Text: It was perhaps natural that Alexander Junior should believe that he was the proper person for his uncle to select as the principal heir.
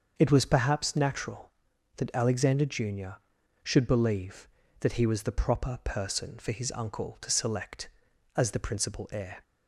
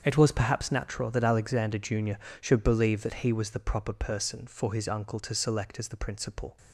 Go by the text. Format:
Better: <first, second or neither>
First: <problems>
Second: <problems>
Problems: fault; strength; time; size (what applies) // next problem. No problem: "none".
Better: first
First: starts louder than the rest; until 1.1 s; 6.5 dB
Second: starts louder than the rest; strong; until 1.0 s; 7.5 dB // stops before "heir"; at 6.5 s